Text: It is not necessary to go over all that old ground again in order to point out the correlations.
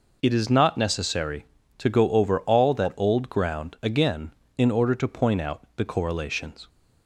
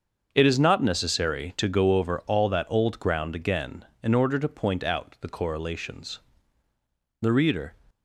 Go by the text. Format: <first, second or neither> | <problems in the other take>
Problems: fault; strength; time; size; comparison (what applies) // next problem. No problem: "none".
first | starts louder than the rest; until 1.3 s; 6.5 dB // goes on to say "The reader"; from 7.1 s on; 0.54 s long